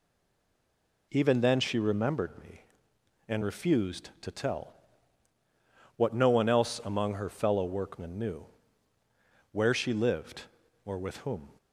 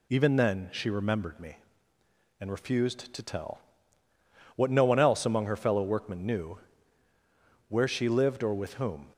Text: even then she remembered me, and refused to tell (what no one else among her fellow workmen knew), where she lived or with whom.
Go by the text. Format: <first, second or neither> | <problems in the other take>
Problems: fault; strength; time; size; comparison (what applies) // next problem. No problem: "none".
second | stays silent before the first word; until 1.1 s; 1.1 s long